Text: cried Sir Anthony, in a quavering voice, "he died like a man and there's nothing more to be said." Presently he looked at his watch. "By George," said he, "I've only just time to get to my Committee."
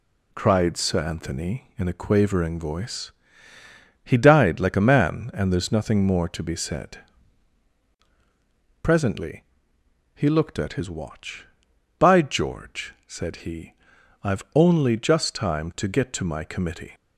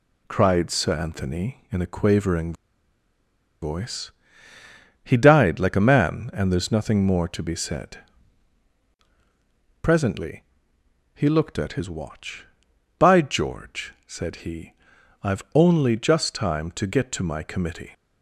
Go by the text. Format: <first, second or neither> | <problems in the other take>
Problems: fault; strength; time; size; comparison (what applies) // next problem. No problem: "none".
first | pauses between "quavering" and "voice"; at 2.5 s; 1.0 s long // pauses between "Presently" and "he"; noticeable; at 10.4 s; 0.72 s long; noticeable in the first